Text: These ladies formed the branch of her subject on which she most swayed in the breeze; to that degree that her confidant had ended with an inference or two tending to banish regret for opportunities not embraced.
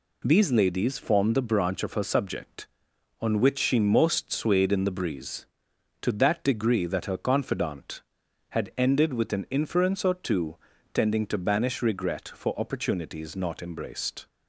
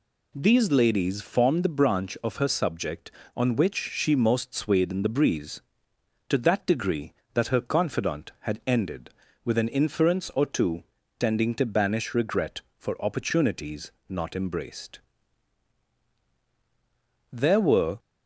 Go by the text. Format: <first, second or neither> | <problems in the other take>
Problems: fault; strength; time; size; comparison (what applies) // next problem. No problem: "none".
first | pauses between "two" and "tending"; slight; at 10.8 s; 0.34 s long; also in the first // pauses between "opportunities" and "not"; slight; at 13.9 s; 0.18 s long // goes on to say "There were"; noticeable; from 17.3 s on; 0.66 s long